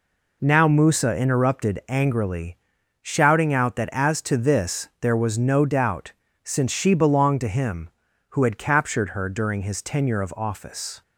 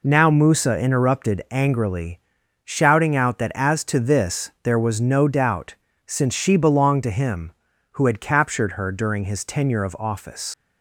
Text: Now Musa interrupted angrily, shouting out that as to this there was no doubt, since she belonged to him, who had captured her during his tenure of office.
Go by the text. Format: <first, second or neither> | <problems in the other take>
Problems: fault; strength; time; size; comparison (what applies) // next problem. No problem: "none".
first | leaves "office" unfinished; at 10.5 s; 105 ms